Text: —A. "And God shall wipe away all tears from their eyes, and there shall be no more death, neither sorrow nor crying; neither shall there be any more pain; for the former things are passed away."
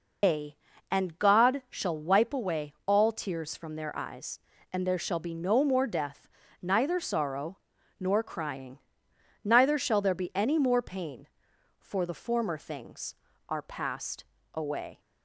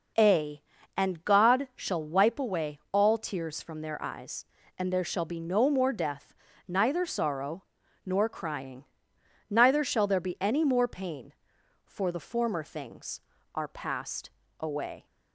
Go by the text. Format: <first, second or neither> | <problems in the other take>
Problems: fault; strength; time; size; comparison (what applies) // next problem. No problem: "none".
second | loses the start of "A"; at 0.2 s; 135 ms // pauses between "sorrow" and "nor"; at 7.5 s; 0.40 s long; also in the second // pauses between "passed" and "away"; slight; at 14.2 s; 0.30 s long; slight in the second